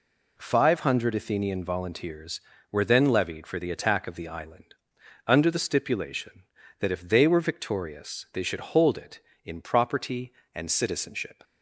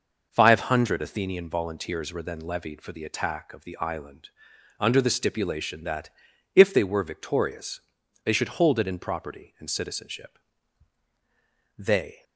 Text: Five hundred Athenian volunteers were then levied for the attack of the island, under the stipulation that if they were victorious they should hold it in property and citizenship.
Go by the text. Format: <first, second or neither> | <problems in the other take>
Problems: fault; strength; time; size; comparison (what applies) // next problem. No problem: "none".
first | pauses between "that" and "if"; at 6.0 s; 0.44 s long // pauses between "victorious" and "they"; at 7.7 s; 0.44 s long // goes on to say "They"; slight; from 11.7 s on; 0.46 s long